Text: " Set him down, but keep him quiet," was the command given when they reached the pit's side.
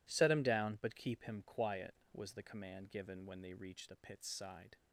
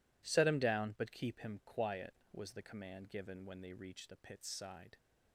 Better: neither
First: none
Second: none

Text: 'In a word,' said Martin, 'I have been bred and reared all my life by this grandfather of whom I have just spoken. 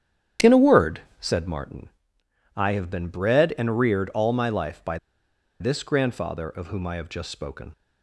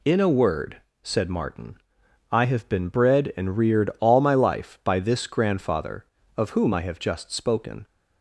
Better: second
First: starts louder than the rest; strong; until 1.6 s; 10 dB // pauses between "by" and "this"; noticeable; at 4.9 s; 0.63 s long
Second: none

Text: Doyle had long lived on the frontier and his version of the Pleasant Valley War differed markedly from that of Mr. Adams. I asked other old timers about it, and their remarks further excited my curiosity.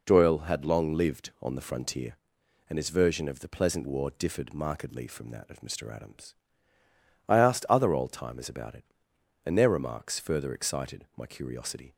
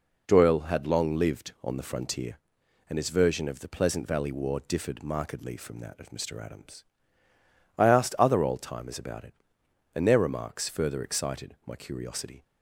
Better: second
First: skips "Valley"; at 3.8 s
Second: none

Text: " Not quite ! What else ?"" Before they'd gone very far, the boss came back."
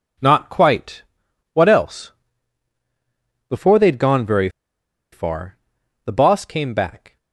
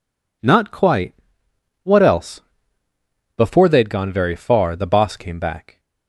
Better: second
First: pauses between "very" and "far"; noticeable; at 4.4 s; 0.63 s long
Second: none

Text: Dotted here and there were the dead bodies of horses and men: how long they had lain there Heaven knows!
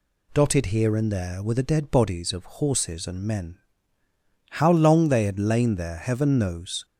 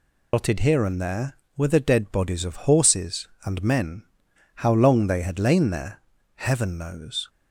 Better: first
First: none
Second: loses the start of "Dotted"; at 0.3 s; 100 ms // pauses between "there" and "Heaven"; slight; at 6.0 s; 0.36 s long

